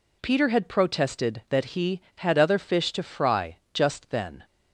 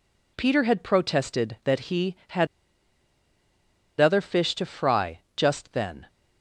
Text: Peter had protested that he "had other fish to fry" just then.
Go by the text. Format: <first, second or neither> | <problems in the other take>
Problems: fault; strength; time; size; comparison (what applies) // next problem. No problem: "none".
first | pauses between "had" and "other"; strong; at 2.4 s; 1.5 s long // pauses between "fry" and "just"; slight; at 5.2 s; 0.16 s long; slight in the first